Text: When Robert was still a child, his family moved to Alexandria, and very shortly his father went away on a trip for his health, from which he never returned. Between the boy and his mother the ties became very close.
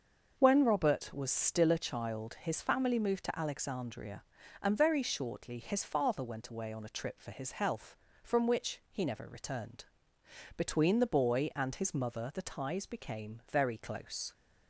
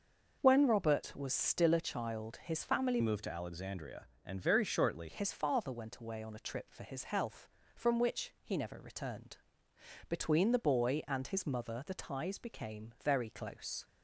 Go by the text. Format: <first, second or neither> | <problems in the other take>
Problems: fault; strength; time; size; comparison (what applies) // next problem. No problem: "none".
first | starts louder than the rest; noticeable; until 1.4 s; 6 dB; also in the first // changes voice from "moved" to "shortly"; from 3.0 to 5.0 s; 2.0 s long